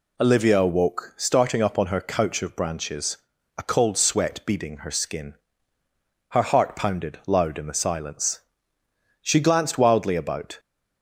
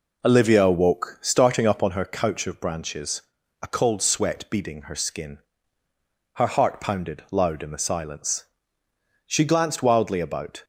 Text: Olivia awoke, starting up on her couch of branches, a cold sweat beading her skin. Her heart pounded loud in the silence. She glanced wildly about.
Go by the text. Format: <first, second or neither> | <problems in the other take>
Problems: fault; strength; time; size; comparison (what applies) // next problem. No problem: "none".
first | starts louder than the rest; noticeable; until 1.9 s; 4 dB